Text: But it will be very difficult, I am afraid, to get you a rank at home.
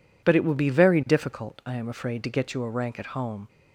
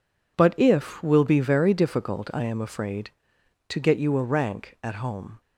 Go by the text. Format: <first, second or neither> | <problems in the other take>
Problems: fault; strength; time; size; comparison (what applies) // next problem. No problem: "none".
first | says "if" for "it"; at 0.5 s